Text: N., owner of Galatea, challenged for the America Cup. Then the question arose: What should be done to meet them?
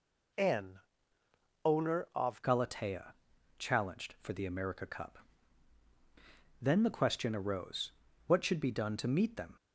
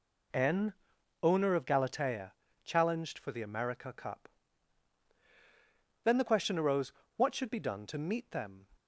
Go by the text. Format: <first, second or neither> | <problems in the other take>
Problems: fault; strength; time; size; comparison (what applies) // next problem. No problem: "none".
second | changes voice at "Galatea"; from 2.4 s on; 7.1 s long